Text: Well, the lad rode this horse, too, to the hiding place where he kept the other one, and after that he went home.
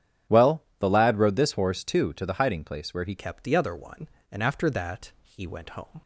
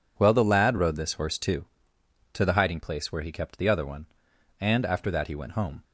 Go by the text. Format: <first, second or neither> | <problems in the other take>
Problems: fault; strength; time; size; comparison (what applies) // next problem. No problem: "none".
second | starts louder than the rest; strong; until 1.4 s; 9.5 dB // changes voice at "kept"; from 3.1 s on; 2.9 s long